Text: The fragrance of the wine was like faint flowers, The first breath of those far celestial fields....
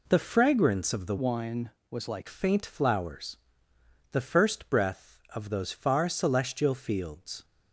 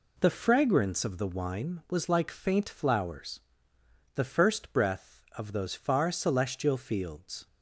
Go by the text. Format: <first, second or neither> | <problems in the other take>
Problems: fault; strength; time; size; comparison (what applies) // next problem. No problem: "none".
second | changes voice from "wine" to "like"; from 1.1 to 2.2 s; 1.1 s long